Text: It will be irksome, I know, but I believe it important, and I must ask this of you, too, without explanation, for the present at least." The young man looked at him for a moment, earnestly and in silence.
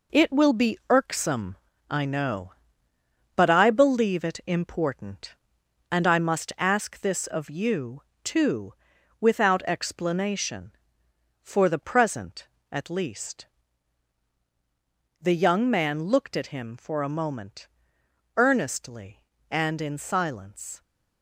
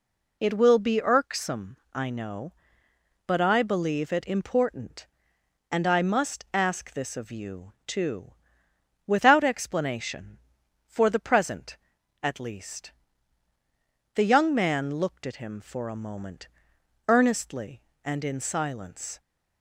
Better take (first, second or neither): second